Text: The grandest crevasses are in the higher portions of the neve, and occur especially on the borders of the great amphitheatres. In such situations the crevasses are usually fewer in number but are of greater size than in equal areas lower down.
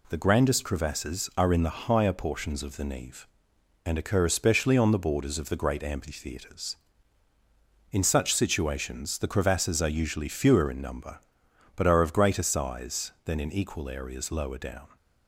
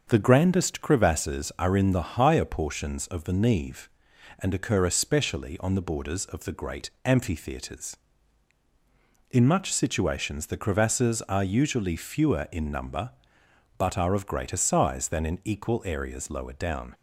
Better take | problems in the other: first | starts louder than the rest; until 1.0 s; 6.5 dB // pauses between "great" and "amphitheatres"; slight; at 6.8 s; 0.16 s long // says "much" for "such"; at 9.4 s

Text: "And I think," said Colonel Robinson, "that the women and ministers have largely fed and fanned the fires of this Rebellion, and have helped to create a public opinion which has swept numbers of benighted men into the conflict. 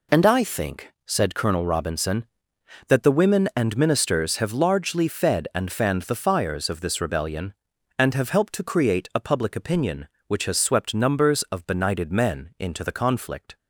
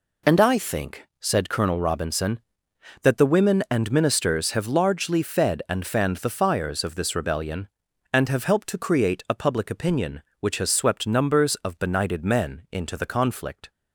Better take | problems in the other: neither | none

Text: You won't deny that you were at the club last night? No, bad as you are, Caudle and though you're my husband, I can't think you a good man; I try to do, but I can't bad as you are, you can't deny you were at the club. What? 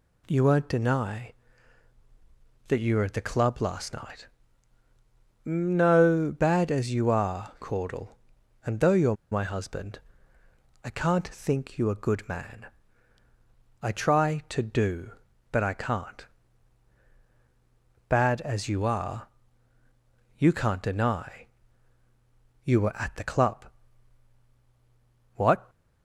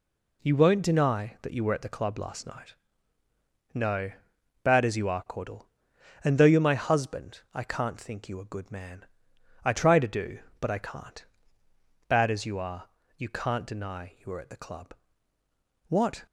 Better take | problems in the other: second | pauses between "you're" and "my"; slight; at 9.1 s; 0.15 s long // pauses between "can't" and "bad"; strong; at 16.2 s; 1.8 s long; noticeable in the second // pauses between "deny" and "you"; at 21.4 s; 1.1 s long

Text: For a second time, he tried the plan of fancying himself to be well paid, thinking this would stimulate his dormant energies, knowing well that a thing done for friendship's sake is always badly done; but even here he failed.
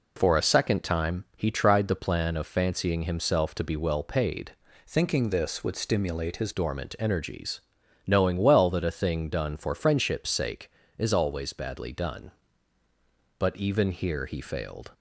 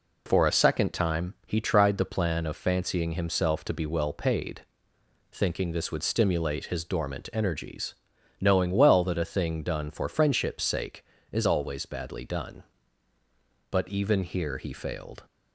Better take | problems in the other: second | changes voice from "thinking" to "his"; from 4.8 to 6.5 s; 1.7 s long

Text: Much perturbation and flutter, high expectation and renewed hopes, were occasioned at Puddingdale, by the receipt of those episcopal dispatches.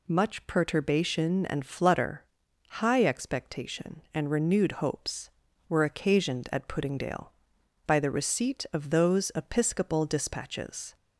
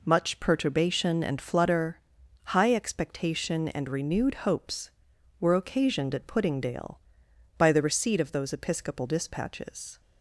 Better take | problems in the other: neither | none

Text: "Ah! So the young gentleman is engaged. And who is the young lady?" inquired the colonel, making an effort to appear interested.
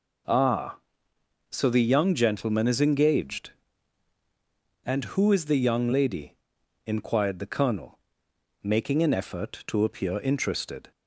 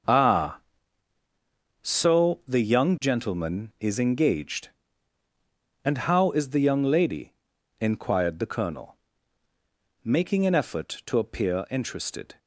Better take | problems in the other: first | starts louder than the rest; until 2.2 s; 6.5 dB // says "how" for "who"; at 5.9 s

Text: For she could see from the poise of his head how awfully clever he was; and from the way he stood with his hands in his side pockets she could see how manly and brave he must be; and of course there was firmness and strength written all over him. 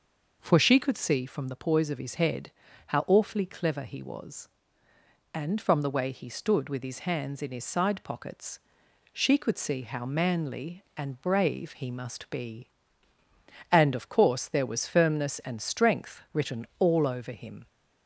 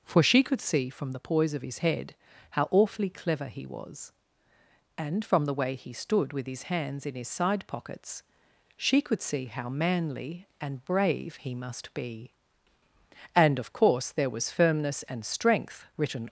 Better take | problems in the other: first | pauses between "head" and "how"; slight; at 2.1 s; 0.36 s long; slight in the first // pauses between "pockets" and "she"; noticeable; at 8.2 s; 0.54 s long; noticeable in the first // stops before "all over him"; at 16.2 s

